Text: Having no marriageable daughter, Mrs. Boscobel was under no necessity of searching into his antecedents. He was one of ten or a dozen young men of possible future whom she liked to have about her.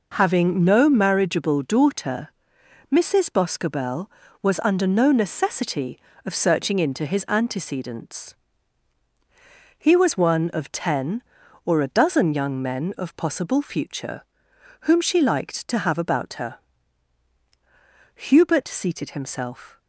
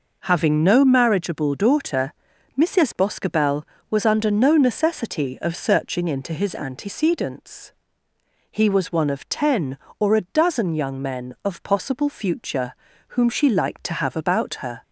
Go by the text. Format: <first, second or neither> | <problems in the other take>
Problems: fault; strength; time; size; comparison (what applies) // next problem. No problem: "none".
second | pauses between "future" and "whom"; noticeable; at 14.2 s; 0.60 s long; slight in the second // goes on to say "Hubert seated himself"; from 18.1 s on; 1.6 s long